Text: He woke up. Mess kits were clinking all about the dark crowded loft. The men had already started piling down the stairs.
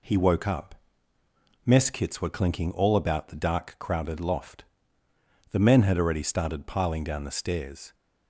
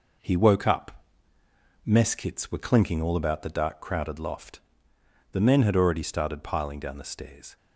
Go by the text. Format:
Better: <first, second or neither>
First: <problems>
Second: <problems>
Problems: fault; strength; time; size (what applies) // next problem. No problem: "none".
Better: first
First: none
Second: gets quieter; noticeable; throughout; 5 dB